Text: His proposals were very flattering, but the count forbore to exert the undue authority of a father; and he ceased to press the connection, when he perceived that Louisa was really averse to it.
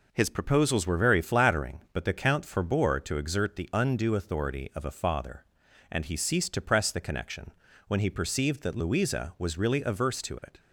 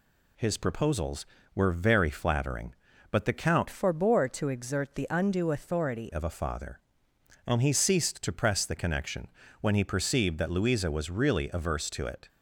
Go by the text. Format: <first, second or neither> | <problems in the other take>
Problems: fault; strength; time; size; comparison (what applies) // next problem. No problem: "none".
first | changes voice from "forbore" to "authority"; from 3.6 to 6.0 s; 2.4 s long